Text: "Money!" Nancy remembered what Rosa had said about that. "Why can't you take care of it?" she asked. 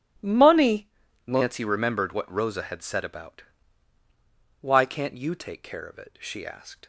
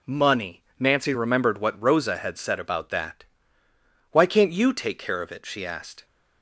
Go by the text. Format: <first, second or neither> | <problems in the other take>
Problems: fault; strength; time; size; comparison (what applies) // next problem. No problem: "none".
second | starts louder than the rest; strong; until 1.5 s; 10 dB // skips "that"; at 4.0 s